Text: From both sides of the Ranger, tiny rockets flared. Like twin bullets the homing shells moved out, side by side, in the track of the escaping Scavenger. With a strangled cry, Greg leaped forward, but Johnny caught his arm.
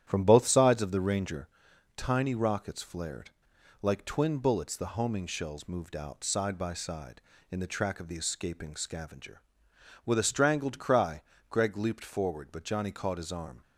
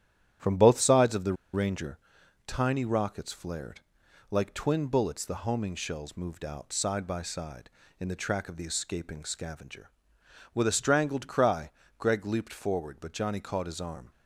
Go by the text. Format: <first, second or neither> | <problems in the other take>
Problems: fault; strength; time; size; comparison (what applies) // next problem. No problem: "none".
first | starts louder than the rest; strong; until 1.6 s; 11 dB; strong in the first // pauses between "the" and "Ranger"; slight; at 1.3 s; 0.18 s long